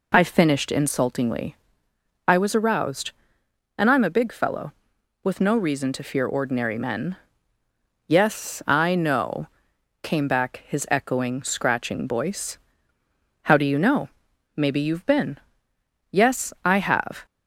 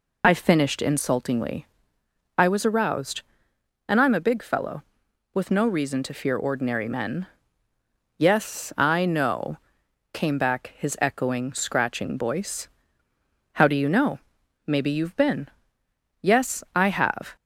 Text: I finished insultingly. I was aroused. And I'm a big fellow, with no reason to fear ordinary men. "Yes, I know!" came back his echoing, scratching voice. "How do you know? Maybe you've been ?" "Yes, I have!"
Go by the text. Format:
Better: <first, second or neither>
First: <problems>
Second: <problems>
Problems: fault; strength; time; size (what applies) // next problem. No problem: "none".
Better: first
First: none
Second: loses the start of "I"; at 0.2 s; 20 ms